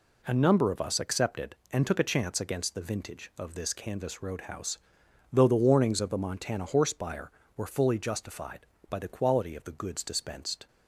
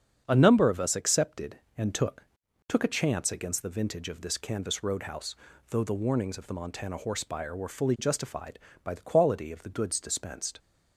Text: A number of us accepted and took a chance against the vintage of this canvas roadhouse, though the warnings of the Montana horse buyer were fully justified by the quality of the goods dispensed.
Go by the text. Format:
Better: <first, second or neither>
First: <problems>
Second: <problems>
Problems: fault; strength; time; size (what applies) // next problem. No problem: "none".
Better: first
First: none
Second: starts louder than the rest; strong; until 1.2 s; 7.5 dB // says "took" twice; at 2.6 s